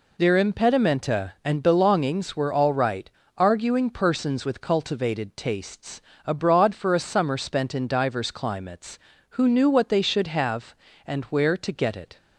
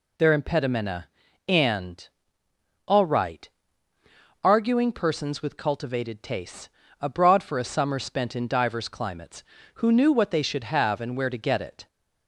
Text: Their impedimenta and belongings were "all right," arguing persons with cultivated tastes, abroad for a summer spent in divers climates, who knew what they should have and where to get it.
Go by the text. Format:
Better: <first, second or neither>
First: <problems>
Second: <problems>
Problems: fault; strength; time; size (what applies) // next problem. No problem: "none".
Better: first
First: none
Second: skips "belongings were"; at 2.4 s